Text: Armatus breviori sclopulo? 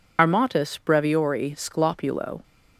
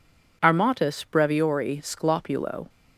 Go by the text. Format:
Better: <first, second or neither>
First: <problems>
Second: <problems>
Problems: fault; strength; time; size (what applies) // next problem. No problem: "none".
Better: second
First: loses the start of "Armatus"; at 0.1 s; 45 ms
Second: none